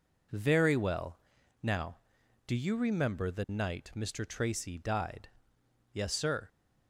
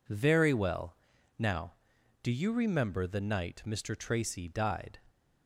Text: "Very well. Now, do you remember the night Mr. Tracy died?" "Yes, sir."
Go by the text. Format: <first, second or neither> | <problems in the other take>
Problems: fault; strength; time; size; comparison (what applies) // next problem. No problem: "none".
first | stops before "Yes sir"; at 5.0 s